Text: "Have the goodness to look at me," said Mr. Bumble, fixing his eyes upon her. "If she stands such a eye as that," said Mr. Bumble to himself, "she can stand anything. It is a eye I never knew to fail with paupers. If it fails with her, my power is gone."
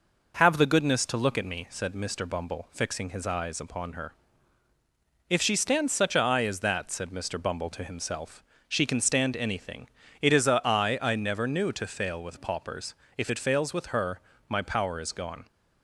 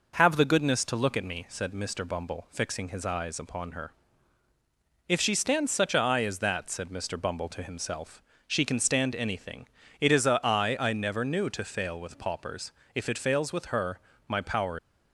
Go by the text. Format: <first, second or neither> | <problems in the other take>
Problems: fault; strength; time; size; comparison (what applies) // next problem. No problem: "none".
first | stops before "is gone"; at 14.7 s